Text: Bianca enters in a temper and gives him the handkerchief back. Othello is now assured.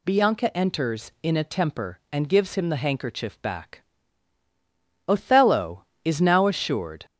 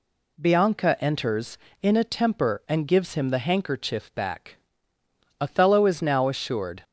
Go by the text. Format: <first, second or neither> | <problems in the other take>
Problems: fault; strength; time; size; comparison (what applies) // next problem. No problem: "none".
second | gets louder; slight; throughout; 3 dB